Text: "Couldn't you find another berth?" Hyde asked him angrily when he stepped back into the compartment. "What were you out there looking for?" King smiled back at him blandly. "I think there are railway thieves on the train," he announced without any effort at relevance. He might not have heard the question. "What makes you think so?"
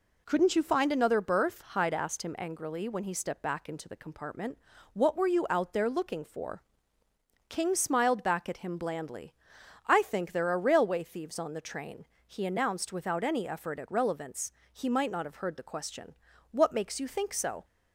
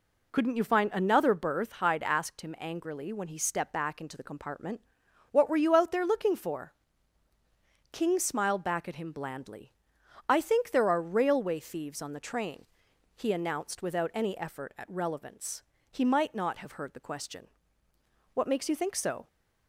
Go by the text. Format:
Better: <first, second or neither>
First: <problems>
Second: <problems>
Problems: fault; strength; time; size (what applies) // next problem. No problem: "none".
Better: neither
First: none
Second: none